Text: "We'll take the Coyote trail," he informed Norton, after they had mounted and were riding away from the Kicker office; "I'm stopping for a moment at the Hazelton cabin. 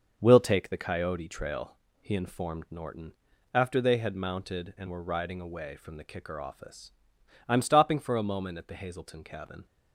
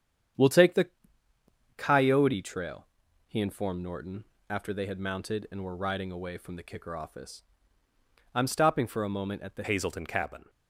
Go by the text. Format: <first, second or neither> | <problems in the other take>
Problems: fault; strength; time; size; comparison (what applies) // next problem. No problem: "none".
first | starts louder than the rest; strong; until 2.2 s; 9 dB; noticeable in the first // pauses between "the" and "Coyote"; noticeable; at 0.8 s; 0.88 s long // changes voice at "Hazelton"; from 9.6 s on; 0.8 s long